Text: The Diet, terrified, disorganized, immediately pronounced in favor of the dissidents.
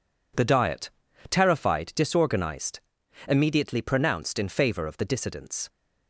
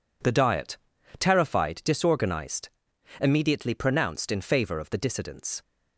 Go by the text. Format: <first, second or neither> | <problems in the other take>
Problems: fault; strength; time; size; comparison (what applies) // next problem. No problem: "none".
neither | none